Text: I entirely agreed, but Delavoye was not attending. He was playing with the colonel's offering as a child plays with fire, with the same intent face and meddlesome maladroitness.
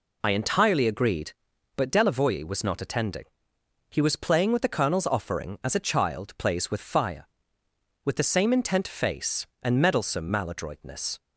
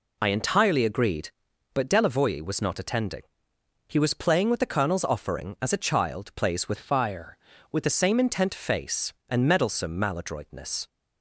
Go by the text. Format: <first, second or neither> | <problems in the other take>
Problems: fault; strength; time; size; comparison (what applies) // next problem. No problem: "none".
first | changes voice from "fire" to "with"; from 6.7 to 7.8 s; 1.1 s long